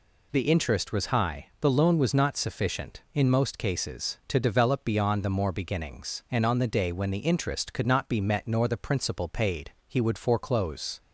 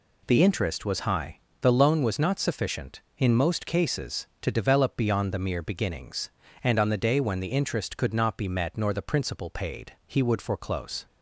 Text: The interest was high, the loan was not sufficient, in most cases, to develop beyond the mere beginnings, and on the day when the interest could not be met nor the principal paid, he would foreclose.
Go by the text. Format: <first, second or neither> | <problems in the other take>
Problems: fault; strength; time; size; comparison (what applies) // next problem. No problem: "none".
second | says "more" for "mere"; at 5.2 s